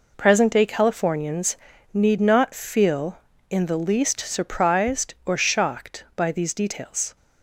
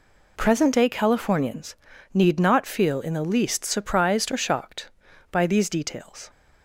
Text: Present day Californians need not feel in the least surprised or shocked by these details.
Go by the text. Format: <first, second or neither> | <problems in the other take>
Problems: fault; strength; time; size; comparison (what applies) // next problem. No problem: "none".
neither | pauses between "Californians" and "need"; the same in both